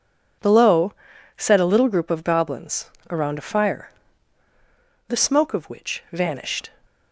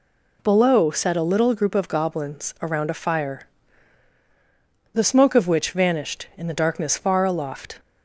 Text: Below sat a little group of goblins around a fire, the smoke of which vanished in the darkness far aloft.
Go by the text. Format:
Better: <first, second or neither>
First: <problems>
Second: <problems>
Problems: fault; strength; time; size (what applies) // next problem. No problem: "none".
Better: second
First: pauses between "Below" and "sat"; at 0.9 s; 0.44 s long // pauses between "goblins" and "around"; slight; at 2.8 s; 0.22 s long // stops before "in the darkness far aloft"; at 6.8 s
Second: none